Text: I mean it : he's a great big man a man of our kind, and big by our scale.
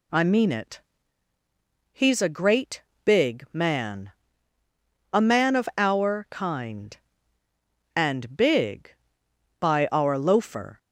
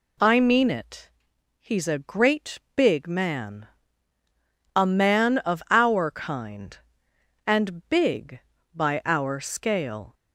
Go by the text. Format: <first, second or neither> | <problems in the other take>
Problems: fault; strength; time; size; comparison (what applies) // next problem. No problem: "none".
second | pauses between "great" and "big"; slight; at 2.8 s; 0.22 s long; slight in the second // pauses between "man" and "a"; at 4.0 s; 1.0 s long; also in the second // says "loafer" for "scale"; at 10.1 s